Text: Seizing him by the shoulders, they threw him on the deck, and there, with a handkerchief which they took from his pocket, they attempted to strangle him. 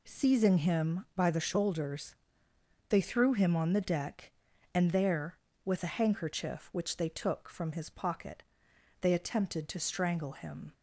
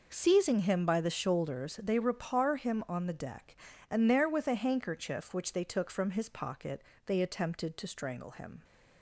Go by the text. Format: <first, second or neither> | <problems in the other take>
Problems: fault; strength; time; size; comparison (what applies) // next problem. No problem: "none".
first | says "repar" for "threw"; at 1.9 s